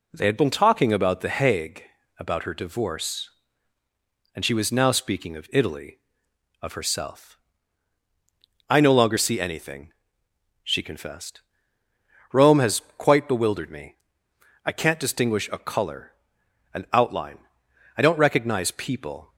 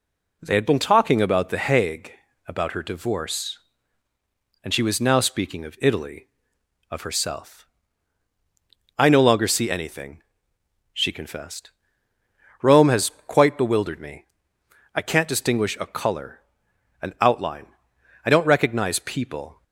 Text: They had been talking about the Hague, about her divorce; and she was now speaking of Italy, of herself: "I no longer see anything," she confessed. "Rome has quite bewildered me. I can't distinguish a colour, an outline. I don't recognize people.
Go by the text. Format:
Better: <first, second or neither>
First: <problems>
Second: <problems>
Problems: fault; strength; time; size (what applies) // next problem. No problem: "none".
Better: neither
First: pauses between "has" and "quite"; slight; at 12.8 s; 0.16 s long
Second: pauses between "has" and "quite"; slight; at 13.1 s; 0.16 s long